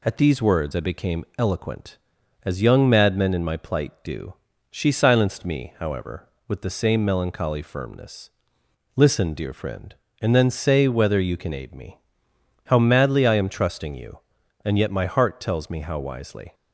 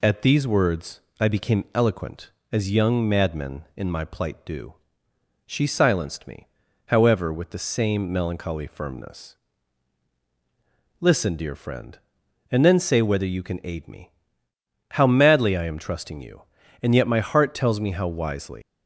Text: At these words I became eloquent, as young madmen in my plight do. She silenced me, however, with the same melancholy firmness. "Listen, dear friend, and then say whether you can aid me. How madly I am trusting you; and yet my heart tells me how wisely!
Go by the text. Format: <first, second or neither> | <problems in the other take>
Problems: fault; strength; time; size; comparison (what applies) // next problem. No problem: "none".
first | pauses between "words" and "I"; slight; at 1.0 s; 0.18 s long // leaves "wisely" unfinished; at 18.6 s; 125 ms